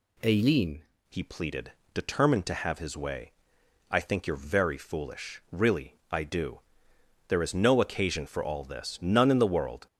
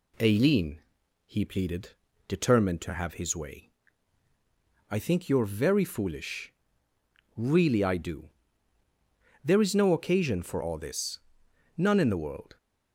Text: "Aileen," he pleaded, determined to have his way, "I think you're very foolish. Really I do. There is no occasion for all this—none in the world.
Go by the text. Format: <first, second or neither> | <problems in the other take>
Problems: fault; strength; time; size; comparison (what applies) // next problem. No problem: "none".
second | changes voice at "he"; from 1.0 s on; 8.8 s long // pauses between "Really" and "I"; slight; at 5.9 s; 0.16 s long